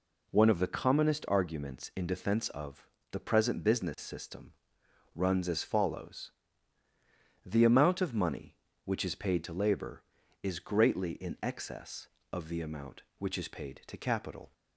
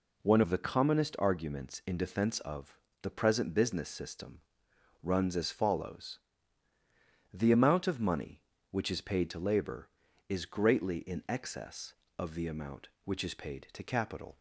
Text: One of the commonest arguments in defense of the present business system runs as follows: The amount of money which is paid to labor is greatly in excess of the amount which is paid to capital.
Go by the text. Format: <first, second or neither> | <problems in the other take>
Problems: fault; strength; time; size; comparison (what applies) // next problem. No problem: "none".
neither | pauses between "of" and "the"; slight; the same in both // pauses between "system" and "runs"; noticeable; the same in both